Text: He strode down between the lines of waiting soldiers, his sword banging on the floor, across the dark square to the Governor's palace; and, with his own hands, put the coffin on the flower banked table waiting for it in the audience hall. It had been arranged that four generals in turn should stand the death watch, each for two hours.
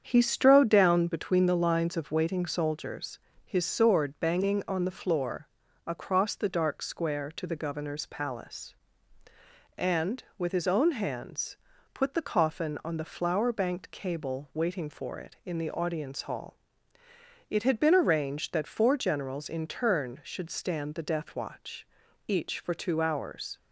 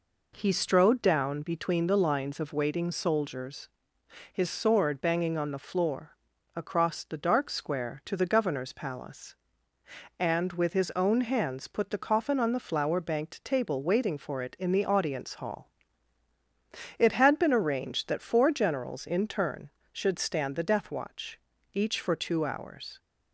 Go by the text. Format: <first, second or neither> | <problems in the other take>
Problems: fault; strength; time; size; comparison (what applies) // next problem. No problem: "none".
second | starts louder than the rest; strong; until 1.0 s; 8 dB // says "cable" for "table"; at 13.9 s